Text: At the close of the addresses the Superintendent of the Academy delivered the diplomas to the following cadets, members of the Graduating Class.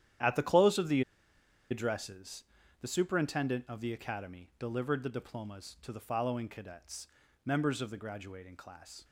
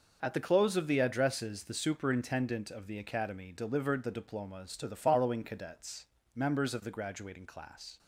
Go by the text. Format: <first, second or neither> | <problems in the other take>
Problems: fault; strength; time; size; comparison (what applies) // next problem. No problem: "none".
second | starts louder than the rest; strong; until 1.9 s; 10.5 dB // pauses between "the" and "addresses"; noticeable; at 1.0 s; 0.69 s long // pauses between "addresses" and "the"; slight; at 2.4 s; 0.36 s long